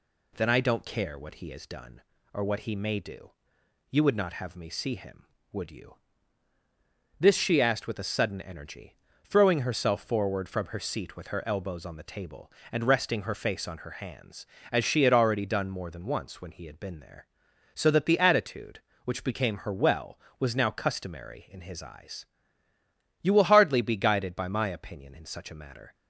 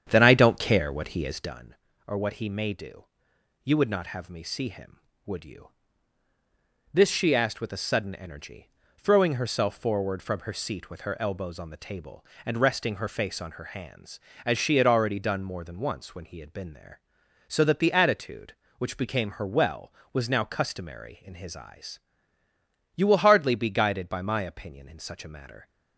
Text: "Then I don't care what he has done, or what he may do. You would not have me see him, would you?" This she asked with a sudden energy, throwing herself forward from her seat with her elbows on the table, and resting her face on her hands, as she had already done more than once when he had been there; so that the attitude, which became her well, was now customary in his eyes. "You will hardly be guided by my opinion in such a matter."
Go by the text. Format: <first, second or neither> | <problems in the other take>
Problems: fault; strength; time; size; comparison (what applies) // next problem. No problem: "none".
first | starts louder than the rest; strong; until 1.6 s; 8.5 dB